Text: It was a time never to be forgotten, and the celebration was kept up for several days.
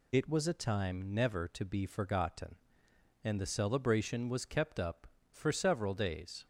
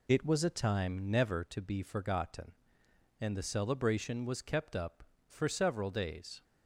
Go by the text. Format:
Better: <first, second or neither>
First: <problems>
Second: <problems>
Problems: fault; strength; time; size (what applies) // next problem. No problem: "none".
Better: first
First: none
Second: starts louder than the rest; slight; until 1.5 s; 2 dB